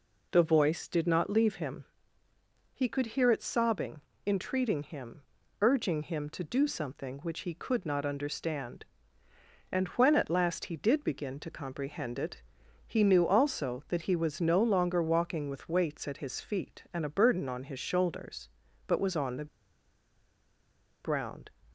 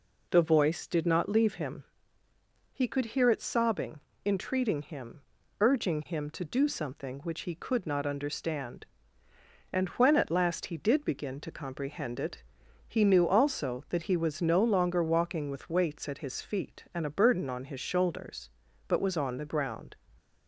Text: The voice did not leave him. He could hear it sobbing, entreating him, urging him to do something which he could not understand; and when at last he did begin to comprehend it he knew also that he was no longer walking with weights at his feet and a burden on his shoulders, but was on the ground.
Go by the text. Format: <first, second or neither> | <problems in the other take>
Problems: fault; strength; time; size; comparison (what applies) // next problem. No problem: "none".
second | pauses between "it" and "he"; at 12.4 s; 0.44 s long; also in the second // pauses between "the" and "ground"; strong; at 19.4 s; 1.5 s long